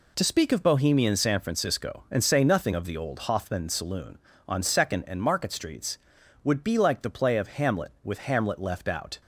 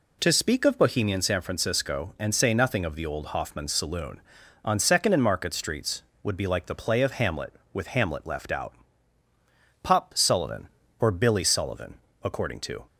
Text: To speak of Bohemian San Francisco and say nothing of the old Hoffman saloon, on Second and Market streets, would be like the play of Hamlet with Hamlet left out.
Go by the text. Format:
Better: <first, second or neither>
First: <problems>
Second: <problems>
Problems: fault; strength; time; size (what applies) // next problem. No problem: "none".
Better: first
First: none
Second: goes on to say "Pop Sullivan or Billy Sullivan according to"; strong; from 9.8 s on; 3.0 s long